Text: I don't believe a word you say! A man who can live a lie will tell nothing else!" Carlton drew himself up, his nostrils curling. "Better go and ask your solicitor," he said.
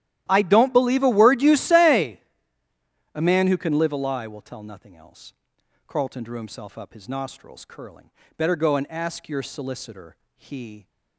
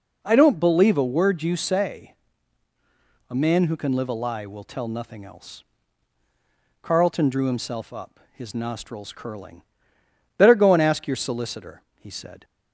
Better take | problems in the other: second | starts louder than the rest; strong; until 1.3 s; 13 dB // stops before "said"; at 10.8 s

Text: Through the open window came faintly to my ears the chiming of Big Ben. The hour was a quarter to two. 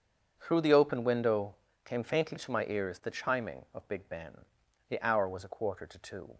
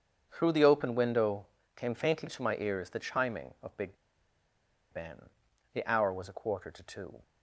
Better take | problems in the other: first | starts louder than the rest; strong; until 1.3 s; 7 dB; strong in the first // pauses between "window" and "came"; slight; at 1.4 s; 0.28 s long; slight in the first // pauses between "Big" and "Ben"; noticeable; at 3.9 s; 0.96 s long

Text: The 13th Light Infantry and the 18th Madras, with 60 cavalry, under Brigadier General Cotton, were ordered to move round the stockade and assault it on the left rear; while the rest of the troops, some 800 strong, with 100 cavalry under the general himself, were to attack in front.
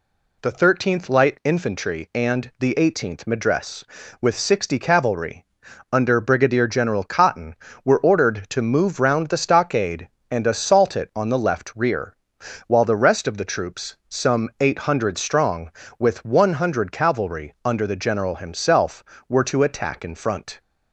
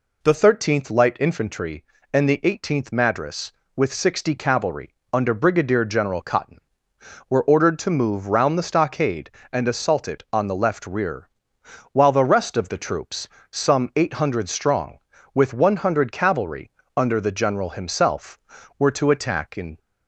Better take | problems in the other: first | pauses between "cavalry" and "under"; slight; at 16.6 s; 0.26 s long // stops before "front"; at 19.7 s

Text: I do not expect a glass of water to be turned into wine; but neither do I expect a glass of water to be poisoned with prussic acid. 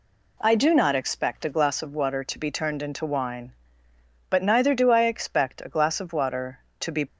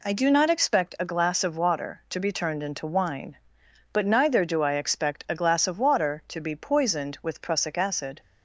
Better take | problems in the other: second | stops before "poisoned with prussic acid"; at 7.0 s

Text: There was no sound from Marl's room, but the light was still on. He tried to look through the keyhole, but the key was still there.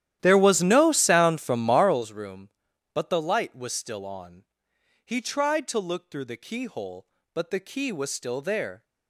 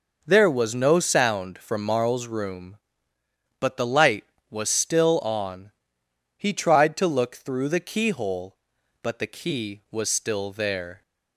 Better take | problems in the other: second | starts louder than the rest; strong; until 2.1 s; 12 dB

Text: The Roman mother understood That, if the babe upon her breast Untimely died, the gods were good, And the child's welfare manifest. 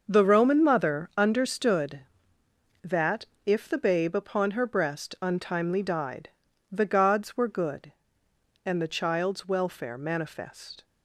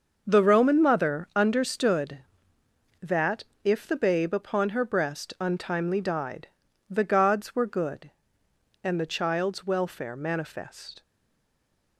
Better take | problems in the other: first | starts louder than the rest; until 1.2 s; 6 dB; also in the first // stays silent after the last word; from 11.0 s on; 0.9 s long

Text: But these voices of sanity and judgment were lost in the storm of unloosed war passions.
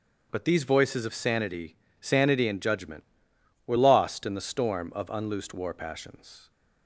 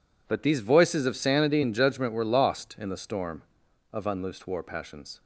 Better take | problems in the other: second | starts louder than the rest; strong; until 1.3 s; 7 dB // says "sanity" twice; at 2.0 s

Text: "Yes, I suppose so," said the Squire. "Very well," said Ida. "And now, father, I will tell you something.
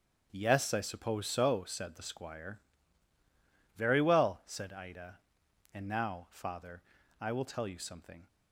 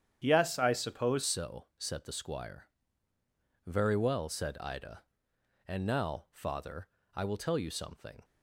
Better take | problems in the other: first | starts louder than the rest; strong; until 1.2 s; 9 dB; strong in the first // changes voice at "so"; from 1.2 s on; 7.0 s long

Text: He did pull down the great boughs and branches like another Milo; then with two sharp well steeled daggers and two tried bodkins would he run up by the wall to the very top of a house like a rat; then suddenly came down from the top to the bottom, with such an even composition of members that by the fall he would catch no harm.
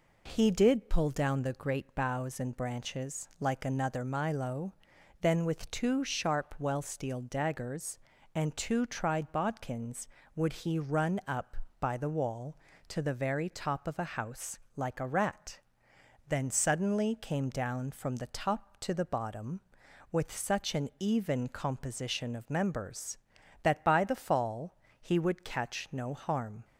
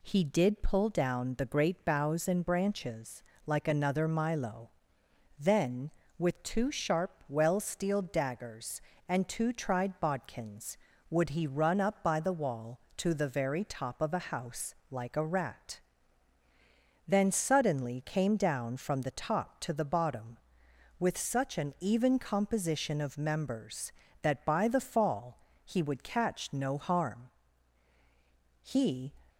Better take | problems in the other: first | pauses between "branches" and "like"; slight; at 3.2 s; 0.24 s long // pauses between "house" and "like"; slight; at 14.7 s; 0.16 s long; slight in the first // pauses between "fall" and "he"; slight; at 25.3 s; 0.26 s long; slight in the first // goes on to say "He"; from 28.6 s on; 0.50 s long

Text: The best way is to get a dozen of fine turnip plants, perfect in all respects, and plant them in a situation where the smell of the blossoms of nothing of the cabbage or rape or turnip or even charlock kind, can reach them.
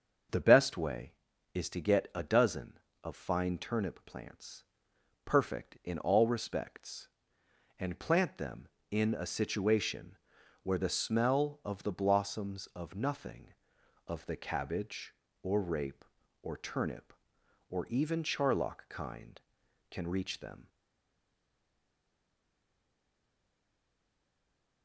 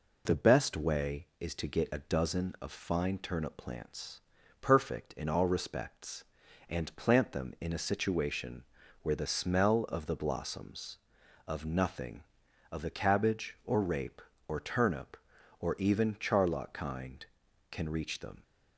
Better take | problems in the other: second | starts louder than the rest; until 1.7 s; 6.5 dB // pauses between "situation" and "where"; noticeable; at 10.1 s; 0.46 s long; also in the second // stays silent after the last word; strong; from 20.6 s on; 4.2 s long

